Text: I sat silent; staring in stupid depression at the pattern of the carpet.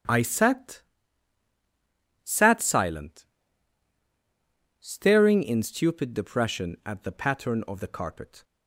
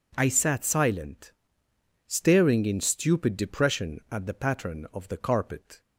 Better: second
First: starts louder than the rest; strong; until 2.5 s; 9.5 dB // says "sat" twice; at 2.2 s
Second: none

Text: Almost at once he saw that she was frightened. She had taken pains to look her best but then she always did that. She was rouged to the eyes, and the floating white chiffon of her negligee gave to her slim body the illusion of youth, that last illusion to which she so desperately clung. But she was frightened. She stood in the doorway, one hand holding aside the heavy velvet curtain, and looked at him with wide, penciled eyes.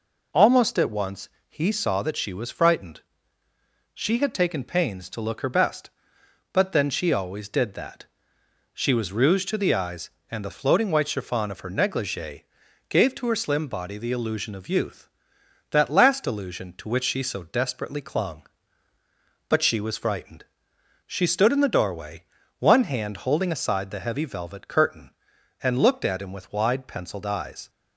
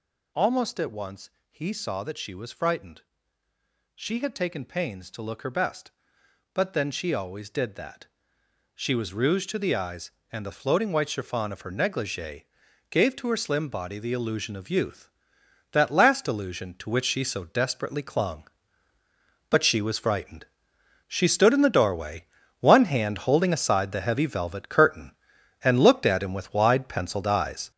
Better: first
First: pauses between "once" and "he"; slight; at 1.2 s; 0.22 s long // pauses between "negligee" and "gave"; noticeable; at 12.4 s; 0.48 s long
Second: gets louder; throughout; 7 dB // pauses between "once" and "he"; slight; at 1.2 s; 0.22 s long // pauses between "negligee" and "gave"; noticeable; at 12.4 s; 0.48 s long

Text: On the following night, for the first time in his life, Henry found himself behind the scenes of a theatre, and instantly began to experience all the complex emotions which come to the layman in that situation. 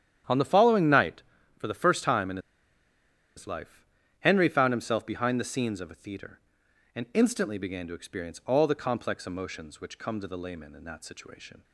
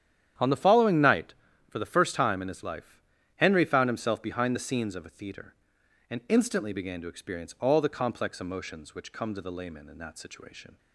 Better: second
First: starts louder than the rest; strong; until 1.6 s; 10 dB // pauses between "in" and "his"; at 2.3 s; 0.98 s long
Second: starts louder than the rest; strong; until 1.7 s; 10 dB

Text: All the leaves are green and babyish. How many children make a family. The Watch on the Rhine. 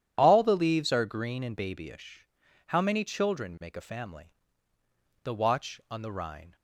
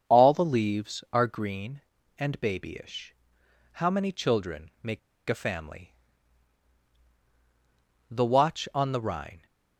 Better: first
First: none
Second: starts louder than the rest; strong; until 1.1 s; 7 dB // pauses between "make" and "a"; slight; at 4.9 s; 0.29 s long

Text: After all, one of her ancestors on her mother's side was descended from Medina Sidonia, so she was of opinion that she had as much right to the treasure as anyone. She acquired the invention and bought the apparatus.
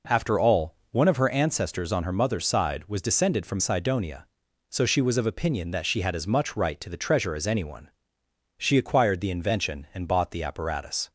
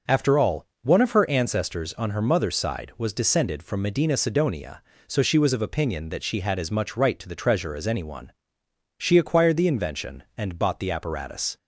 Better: second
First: skips "Medina"; at 3.5 s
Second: none

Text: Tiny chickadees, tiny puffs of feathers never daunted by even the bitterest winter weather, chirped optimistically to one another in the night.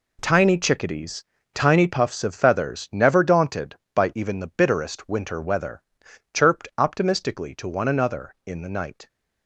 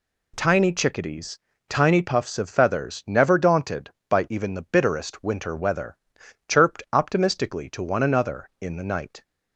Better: second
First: gets quieter; strong; throughout; 11 dB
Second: none

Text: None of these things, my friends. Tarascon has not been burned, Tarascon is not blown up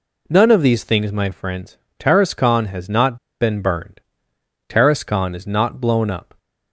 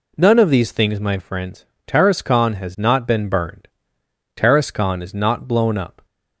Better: second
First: pauses between "not" and "been"; slight; at 3.1 s; 0.25 s long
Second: none

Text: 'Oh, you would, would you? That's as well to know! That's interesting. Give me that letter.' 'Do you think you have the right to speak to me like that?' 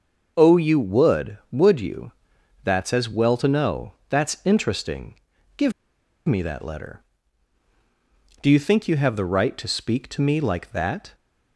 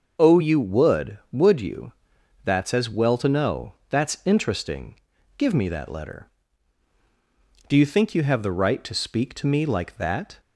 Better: second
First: starts louder than the rest; noticeable; until 1.3 s; 6 dB // pauses between "Give" and "me"; noticeable; at 5.7 s; 0.54 s long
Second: starts louder than the rest; until 1.3 s; 6 dB

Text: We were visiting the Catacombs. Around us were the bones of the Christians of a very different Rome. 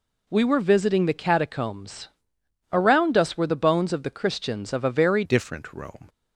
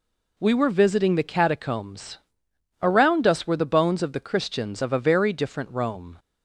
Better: second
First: changes voice at "different"; from 5.2 s on; 0.8 s long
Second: none

